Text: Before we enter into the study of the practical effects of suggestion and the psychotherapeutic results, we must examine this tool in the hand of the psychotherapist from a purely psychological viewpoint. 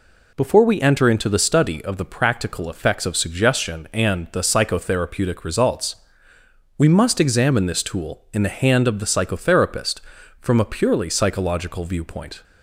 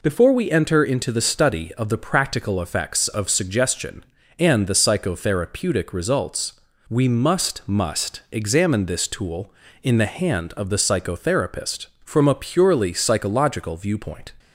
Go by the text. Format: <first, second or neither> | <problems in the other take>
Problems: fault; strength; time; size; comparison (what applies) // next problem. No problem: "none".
first | says "must" twice; at 7.6 s